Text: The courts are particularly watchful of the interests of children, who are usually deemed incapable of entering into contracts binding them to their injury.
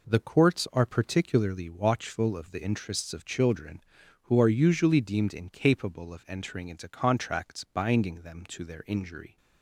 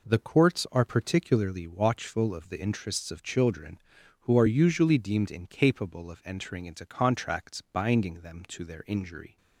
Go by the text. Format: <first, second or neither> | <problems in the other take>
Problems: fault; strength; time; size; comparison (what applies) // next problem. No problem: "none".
neither | none